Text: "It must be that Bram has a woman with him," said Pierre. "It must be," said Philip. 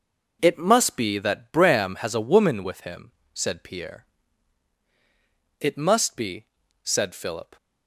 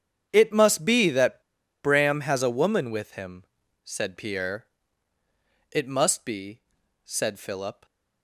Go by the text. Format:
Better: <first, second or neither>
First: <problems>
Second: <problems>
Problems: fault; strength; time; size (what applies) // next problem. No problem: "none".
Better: first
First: none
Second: starts louder than the rest; strong; until 1.3 s; 8.5 dB // pauses between "that" and "Bram"; at 1.4 s; 0.42 s long